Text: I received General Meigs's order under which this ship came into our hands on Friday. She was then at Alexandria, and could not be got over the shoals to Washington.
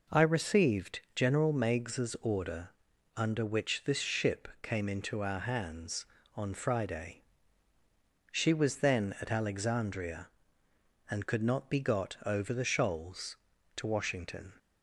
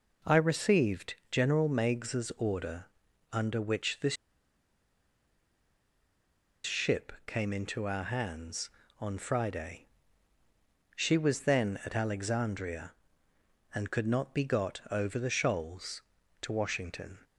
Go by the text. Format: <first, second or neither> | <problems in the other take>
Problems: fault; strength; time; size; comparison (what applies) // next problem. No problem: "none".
first | pauses between "received" and "General"; slight; at 1.1 s; 0.16 s long // pauses between "order" and "under"; noticeable; at 2.8 s; 0.48 s long; noticeable in the first // pauses between "this" and "ship"; strong; at 4.1 s; 2.5 s long // pauses between "ship" and "came"; slight; at 7.1 s; 0.16 s long; slight in the first